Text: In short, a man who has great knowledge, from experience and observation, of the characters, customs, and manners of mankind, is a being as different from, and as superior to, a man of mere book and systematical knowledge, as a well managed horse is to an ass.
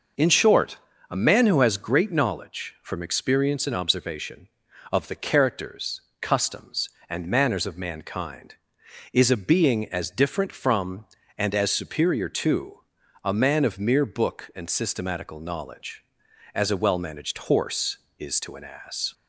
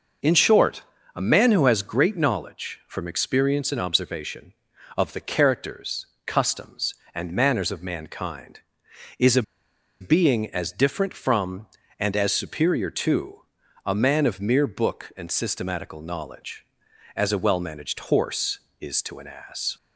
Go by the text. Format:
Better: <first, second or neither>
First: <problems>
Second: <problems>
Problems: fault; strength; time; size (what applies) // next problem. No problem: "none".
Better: first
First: none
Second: pauses between "a" and "being"; noticeable; at 9.4 s; 0.57 s long